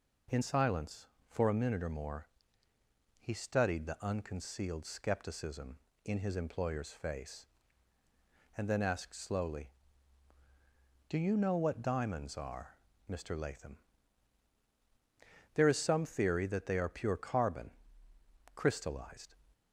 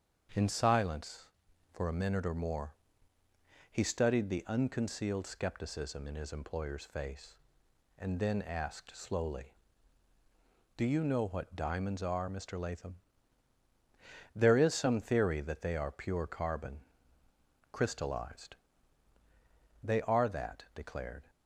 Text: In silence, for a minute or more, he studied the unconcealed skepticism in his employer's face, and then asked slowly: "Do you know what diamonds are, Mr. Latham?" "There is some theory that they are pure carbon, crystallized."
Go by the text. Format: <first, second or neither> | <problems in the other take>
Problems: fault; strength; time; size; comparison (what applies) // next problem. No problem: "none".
first | starts louder than the rest; strong; until 1.8 s; 7.5 dB // goes on to say "They are that declared"; from 19.8 s on; 1.4 s long